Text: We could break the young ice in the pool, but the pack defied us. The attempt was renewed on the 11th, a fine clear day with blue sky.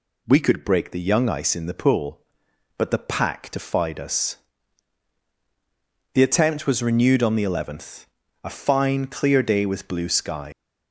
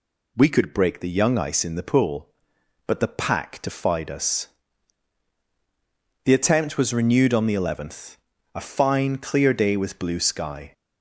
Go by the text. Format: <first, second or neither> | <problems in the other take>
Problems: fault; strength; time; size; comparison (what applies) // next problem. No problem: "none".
second | leaves "sky" unfinished; at 10.5 s; 95 ms